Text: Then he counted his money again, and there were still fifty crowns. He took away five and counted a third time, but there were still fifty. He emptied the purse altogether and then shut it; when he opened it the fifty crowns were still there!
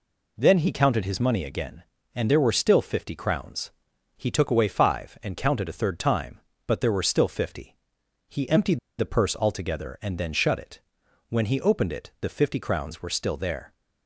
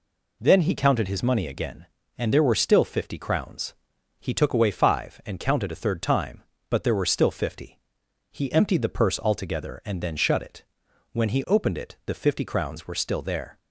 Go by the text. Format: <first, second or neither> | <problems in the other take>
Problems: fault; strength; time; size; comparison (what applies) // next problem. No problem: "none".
second | pauses between "emptied" and "the"; slight; at 8.7 s; 0.20 s long